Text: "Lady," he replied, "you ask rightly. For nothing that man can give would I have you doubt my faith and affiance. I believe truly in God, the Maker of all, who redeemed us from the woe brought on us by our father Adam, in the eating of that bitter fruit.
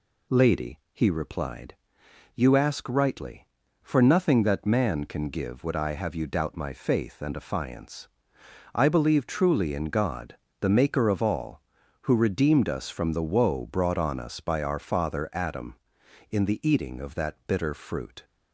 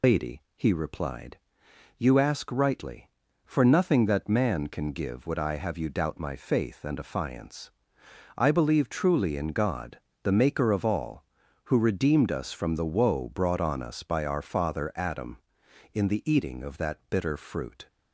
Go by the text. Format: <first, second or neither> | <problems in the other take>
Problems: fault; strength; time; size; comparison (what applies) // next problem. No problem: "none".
first | loses the start of "Lady"; at 0.0 s; 110 ms